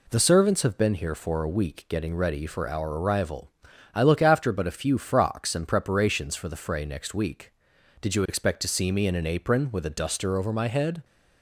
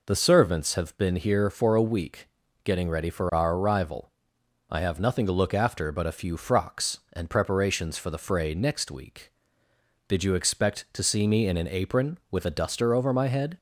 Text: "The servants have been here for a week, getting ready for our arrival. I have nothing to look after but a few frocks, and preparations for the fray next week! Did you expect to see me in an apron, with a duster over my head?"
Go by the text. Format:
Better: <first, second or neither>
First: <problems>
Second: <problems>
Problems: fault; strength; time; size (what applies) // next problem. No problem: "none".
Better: second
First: skips "have nothing to"; at 4.0 s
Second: none